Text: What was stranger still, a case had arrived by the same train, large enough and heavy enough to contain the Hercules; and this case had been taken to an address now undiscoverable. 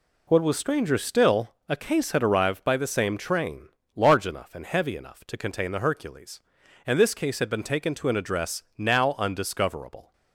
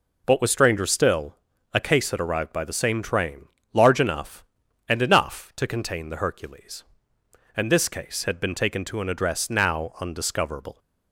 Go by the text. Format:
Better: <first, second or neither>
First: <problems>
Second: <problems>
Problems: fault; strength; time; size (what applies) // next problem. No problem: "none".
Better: first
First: none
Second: skips "heavy"; at 5.0 s